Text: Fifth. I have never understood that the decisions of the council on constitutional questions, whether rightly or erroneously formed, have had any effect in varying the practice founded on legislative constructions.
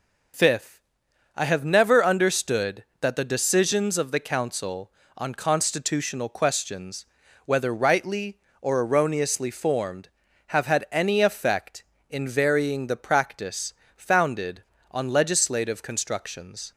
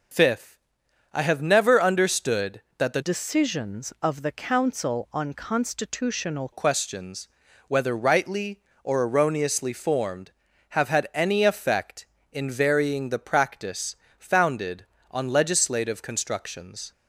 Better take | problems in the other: first | changes voice from "decisions" to "constitutional"; from 3.0 to 6.5 s; 3.5 s long // pauses between "practice" and "founded"; slight; at 13.9 s; 0.22 s long; slight in the first

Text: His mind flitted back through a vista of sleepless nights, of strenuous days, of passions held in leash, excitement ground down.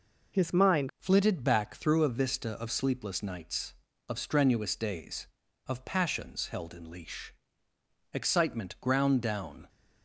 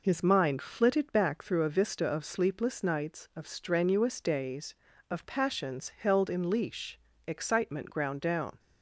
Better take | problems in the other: second | changes voice at "flitted"; from 0.9 s on; 8.7 s long

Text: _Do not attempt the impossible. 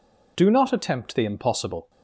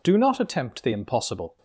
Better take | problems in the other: neither | none

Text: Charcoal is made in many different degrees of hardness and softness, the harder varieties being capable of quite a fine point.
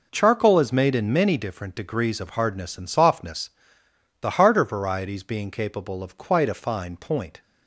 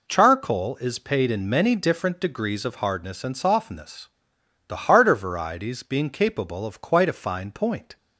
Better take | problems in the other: first | says "paid" for "made"; at 0.9 s

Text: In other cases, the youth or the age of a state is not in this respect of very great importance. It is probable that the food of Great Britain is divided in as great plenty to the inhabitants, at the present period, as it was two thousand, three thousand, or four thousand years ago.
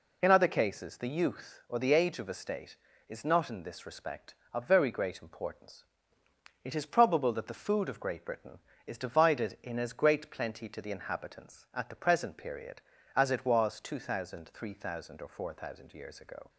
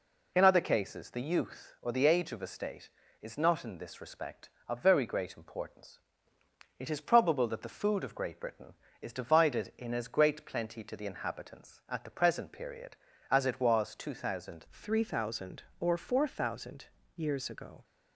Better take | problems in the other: first | changes voice at "three"; from 14.7 s on; 3.1 s long // pauses between "thousand" and "years"; slight; at 16.8 s; 0.30 s long

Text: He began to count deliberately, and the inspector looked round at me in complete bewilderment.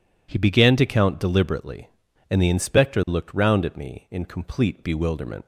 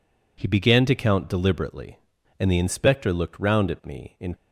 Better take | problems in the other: first | stops before "complete bewilderment"; at 4.3 s

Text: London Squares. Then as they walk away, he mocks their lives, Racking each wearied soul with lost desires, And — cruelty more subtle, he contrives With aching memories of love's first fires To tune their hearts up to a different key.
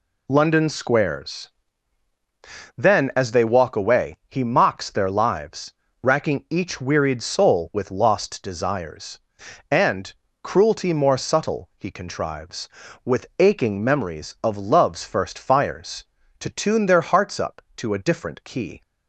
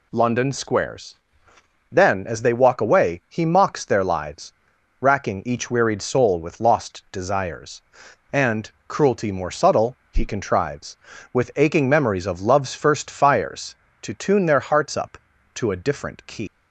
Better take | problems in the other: first | leaves "key" unfinished; at 16.4 s; 135 ms

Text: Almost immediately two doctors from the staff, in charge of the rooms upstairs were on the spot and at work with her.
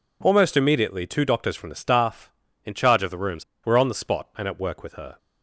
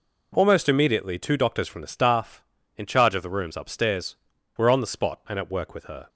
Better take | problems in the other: second | skips "upstairs"; at 3.5 s

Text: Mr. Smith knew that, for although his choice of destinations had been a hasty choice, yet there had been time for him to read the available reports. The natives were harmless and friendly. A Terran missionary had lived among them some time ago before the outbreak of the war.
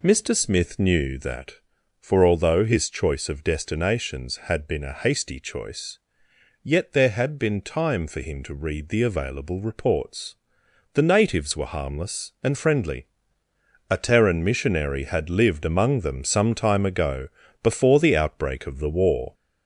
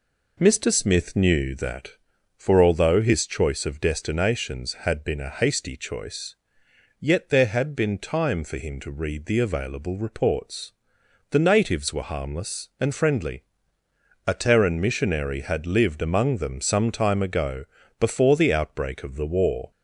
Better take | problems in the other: second | gets louder; slight; throughout; 2 dB // pauses between "ago" and "before"; slight; at 17.2 s; 0.34 s long; slight in the second

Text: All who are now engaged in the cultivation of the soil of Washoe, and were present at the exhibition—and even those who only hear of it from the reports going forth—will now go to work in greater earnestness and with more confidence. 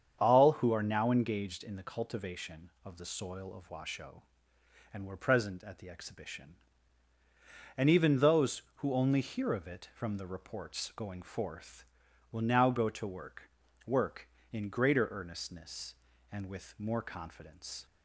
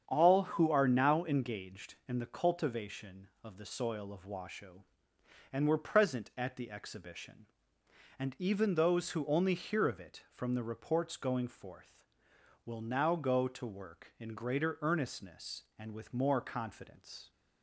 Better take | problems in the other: second | starts louder than the rest; strong; until 1.2 s; 8 dB; strong in the second // says "work" twice; at 13.8 s

